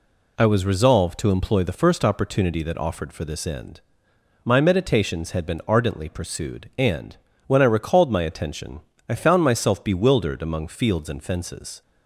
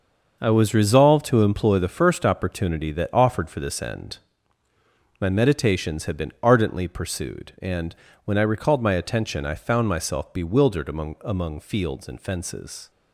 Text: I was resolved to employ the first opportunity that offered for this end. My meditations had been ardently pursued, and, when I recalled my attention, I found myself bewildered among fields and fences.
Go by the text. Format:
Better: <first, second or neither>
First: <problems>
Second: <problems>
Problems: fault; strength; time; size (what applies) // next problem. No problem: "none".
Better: first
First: none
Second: starts louder than the rest; until 1.4 s; 6 dB // says "among" twice; at 11.2 s